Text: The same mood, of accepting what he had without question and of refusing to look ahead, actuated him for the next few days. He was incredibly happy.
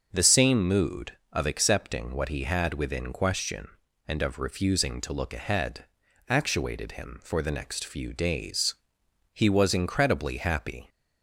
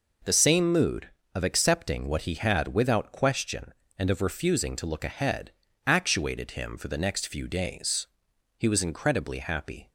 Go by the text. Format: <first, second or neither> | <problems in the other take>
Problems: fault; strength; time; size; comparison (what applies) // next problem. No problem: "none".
second | says "within" for "without"; at 2.7 s